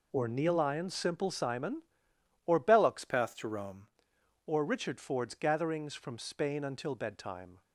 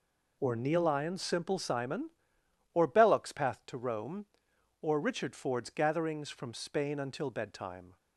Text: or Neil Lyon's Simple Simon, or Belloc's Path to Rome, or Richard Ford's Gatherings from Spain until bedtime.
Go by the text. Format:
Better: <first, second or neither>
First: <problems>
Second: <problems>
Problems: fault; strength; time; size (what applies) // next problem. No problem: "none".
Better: second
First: changes voice from "Path" to "Rome"; from 3.0 to 3.8 s; 0.8 s long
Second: none